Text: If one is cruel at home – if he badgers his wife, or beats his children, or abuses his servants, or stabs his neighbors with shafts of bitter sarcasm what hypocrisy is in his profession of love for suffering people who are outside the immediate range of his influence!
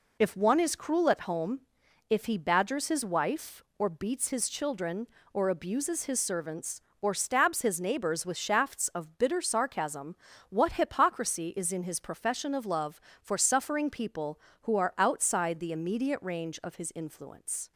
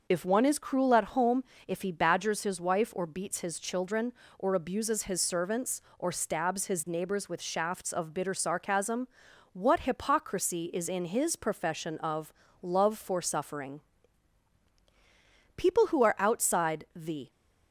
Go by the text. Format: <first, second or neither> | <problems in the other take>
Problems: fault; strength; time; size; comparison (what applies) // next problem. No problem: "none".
first | pauses between "sarcasm" and "what"; noticeable; at 9.0 s; 0.46 s long; slight in the first // pauses between "of" and "love"; slight; at 12.3 s; 0.30 s long // pauses between "suffering" and "people"; strong; at 13.8 s; 1.7 s long // stops before "immediate range of his influence"; at 17.3 s